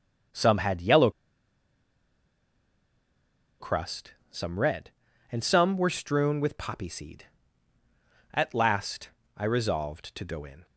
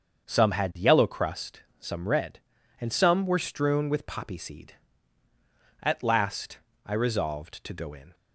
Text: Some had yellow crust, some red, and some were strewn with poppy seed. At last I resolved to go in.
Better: second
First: starts louder than the rest; until 3.8 s; 7 dB // pauses between "yellow" and "crust"; strong; at 1.0 s; 2.5 s long // pauses between "last" and "I"; slight; at 9.0 s; 0.26 s long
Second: starts louder than the rest; until 1.2 s; 7 dB // pauses between "last" and "I"; slight; at 6.5 s; 0.26 s long

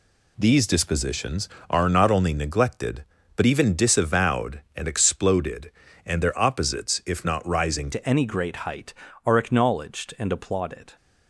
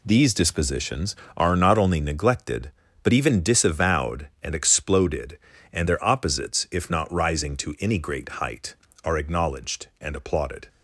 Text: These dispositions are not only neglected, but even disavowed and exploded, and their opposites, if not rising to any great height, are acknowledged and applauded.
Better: second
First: changes voice at "to"; from 7.9 s on; 3.0 s long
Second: none

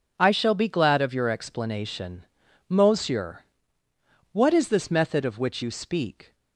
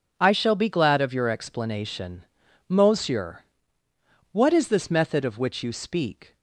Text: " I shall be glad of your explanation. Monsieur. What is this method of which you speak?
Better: neither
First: none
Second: none

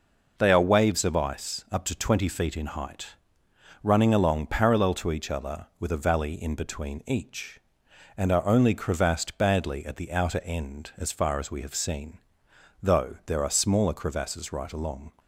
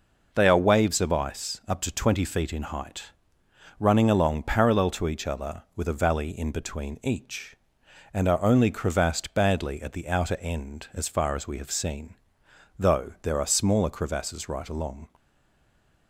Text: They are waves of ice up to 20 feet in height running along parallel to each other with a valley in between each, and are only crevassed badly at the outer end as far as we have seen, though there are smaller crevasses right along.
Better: first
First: pauses between "height" and "running"; noticeable; at 3.0 s; 0.78 s long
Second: pauses between "height" and "running"; noticeable; at 3.0 s; 0.78 s long // stays silent after the last word; slight; from 15.1 s on; 0.9 s long

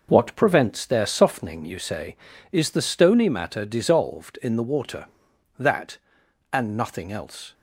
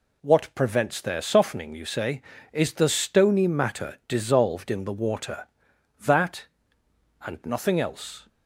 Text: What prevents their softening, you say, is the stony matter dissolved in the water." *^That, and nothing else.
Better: second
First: gets quieter; throughout; 6.5 dB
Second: none

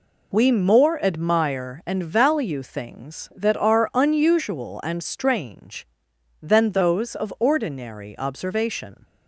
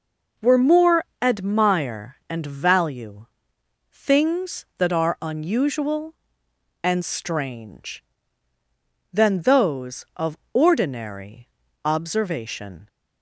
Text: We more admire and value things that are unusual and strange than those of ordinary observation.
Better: first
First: none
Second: says "Were" for "We"; at 0.3 s // pauses between "more" and "admire"; slight; at 1.0 s; 0.16 s long // pauses between "value" and "things"; noticeable; at 3.2 s; 0.66 s long // pauses between "of" and "ordinary"; slight; at 10.3 s; 0.16 s long // pauses between "ordinary" and "observation"; slight; at 11.4 s; 0.34 s long

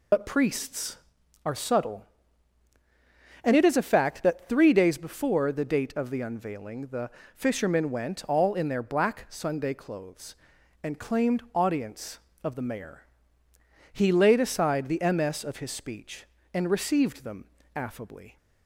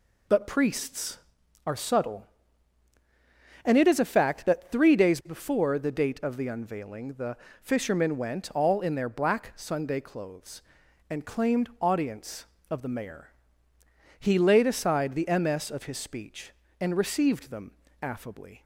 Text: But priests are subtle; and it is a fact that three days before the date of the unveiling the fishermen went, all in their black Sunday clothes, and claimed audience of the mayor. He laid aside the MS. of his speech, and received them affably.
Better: second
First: loses the start of "But"; at 0.1 s; 40 ms // pauses between "the" and "fishermen"; slight; at 7.1 s; 0.24 s long // pauses between "them" and "affably"; slight; at 17.4 s; 0.30 s long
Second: pauses between "the" and "fishermen"; slight; at 7.3 s; 0.24 s long // pauses between "them" and "affably"; slight; at 17.7 s; 0.30 s long

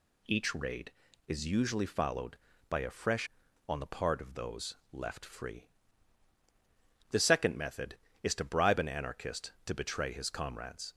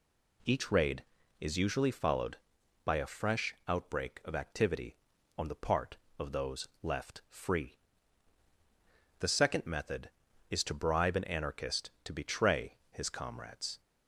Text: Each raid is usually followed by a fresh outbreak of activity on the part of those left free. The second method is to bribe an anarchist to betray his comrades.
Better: second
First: skips "outbreak of activity"; at 3.4 s // pauses between "those" and "left"; slight; at 4.7 s; 0.16 s long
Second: none

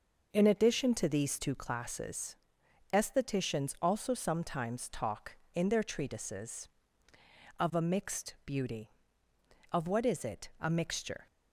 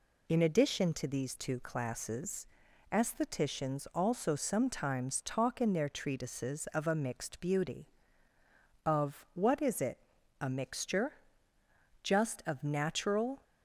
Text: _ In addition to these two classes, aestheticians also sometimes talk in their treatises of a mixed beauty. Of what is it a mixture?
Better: first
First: none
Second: pauses between "it" and "a"; at 9.9 s; 0.42 s long // goes on to say "Just of natural"; from 12.0 s on; 1.4 s long

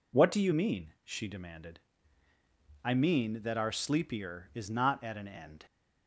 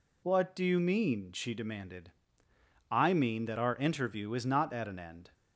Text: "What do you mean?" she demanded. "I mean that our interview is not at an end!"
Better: second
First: says "sleepier" for "interview"; at 3.7 s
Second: none

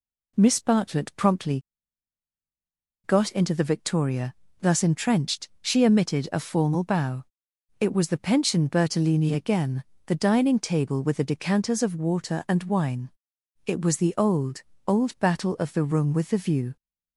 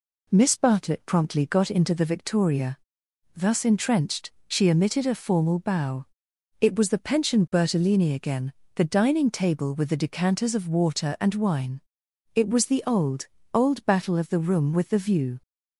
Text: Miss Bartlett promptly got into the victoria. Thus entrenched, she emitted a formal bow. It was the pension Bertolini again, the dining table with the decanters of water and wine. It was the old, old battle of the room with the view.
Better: second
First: pauses between "promptly" and "got"; strong; at 1.6 s; 1.4 s long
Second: none

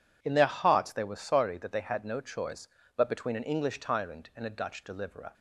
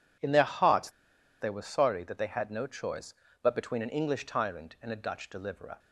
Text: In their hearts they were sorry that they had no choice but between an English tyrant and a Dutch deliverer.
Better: first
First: none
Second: pauses between "hearts" and "they"; noticeable; at 0.8 s; 0.50 s long

